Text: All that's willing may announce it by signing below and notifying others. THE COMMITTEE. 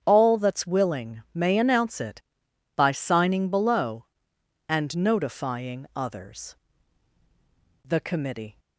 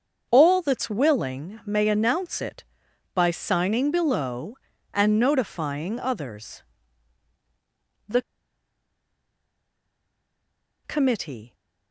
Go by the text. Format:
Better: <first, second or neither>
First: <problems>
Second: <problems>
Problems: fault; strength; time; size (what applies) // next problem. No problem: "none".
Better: first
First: starts louder than the rest; strong; until 1.0 s; 8 dB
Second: starts louder than the rest; until 1.3 s; 7 dB // pauses between "THE" and "COMMITTEE"; strong; at 8.1 s; 2.6 s long